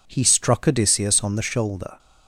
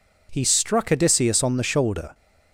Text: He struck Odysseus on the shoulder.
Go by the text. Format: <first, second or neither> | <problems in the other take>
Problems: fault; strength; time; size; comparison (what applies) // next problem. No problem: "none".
neither | none